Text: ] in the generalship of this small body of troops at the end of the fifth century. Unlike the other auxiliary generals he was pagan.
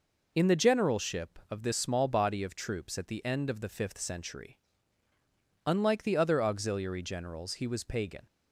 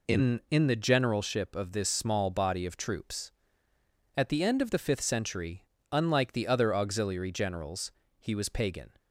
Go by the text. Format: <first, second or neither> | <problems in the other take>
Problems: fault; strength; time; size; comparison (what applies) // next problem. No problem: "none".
first | says "in" twice; at 0.5 s // pauses between "generals" and "he"; slight; at 7.9 s; 0.28 s long